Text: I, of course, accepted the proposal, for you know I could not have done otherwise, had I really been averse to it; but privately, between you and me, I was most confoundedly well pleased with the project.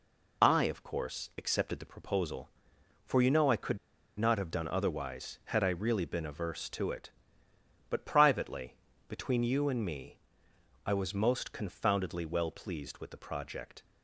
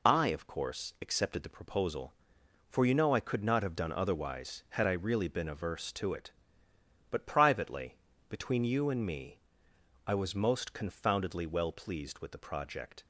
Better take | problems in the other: second | pauses between "could" and "not"; at 3.7 s; 0.40 s long

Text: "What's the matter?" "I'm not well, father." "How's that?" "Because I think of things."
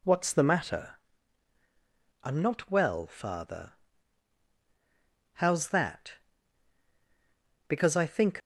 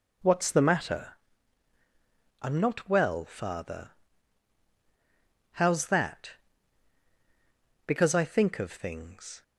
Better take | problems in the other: second | stops before "of things"; at 8.4 s

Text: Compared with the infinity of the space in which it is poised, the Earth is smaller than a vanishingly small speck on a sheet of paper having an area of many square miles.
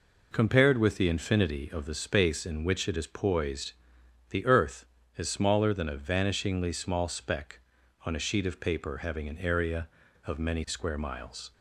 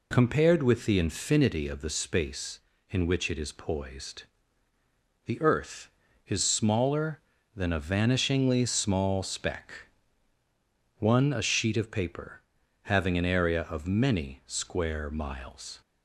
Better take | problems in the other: first | says "one" for "on"; at 10.9 s // pauses between "paper" and "having"; at 12.4 s; 0.42 s long

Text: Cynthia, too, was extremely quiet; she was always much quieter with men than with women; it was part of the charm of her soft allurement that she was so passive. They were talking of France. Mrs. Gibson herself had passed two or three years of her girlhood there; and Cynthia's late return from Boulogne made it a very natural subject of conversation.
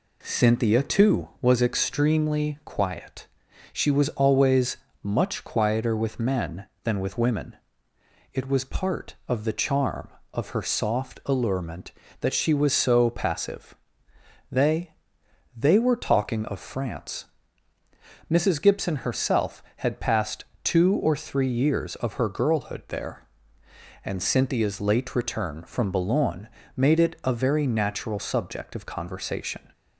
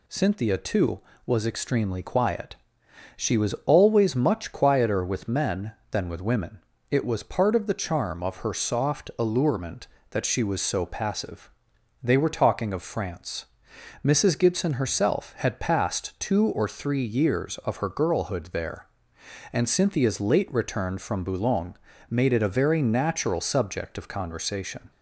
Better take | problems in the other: second | pauses between "always" and "much"; slight; at 4.7 s; 0.24 s long // says "They" twice; at 15.5 s // pauses between "passed" and "two"; slight; at 20.4 s; 0.18 s long // pauses between "Boulogne" and "made"; slight; at 26.4 s; 0.28 s long; slight in the second

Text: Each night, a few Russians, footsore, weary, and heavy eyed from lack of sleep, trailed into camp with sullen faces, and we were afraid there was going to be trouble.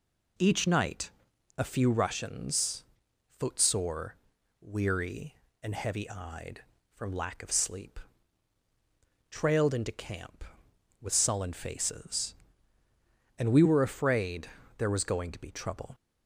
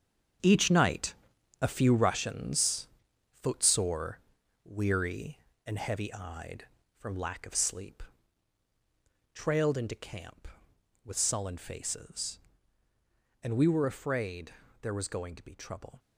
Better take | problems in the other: first | gets quieter; strong; throughout; 11 dB // pauses between "afraid" and "there"; slight; at 14.5 s; 0.28 s long; slight in the first

